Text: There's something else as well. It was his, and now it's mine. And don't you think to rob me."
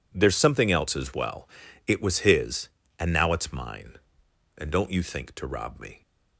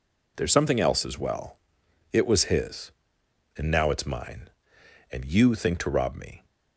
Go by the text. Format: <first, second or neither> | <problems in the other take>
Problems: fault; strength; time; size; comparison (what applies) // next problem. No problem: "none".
first | skips "don't"; at 5.2 s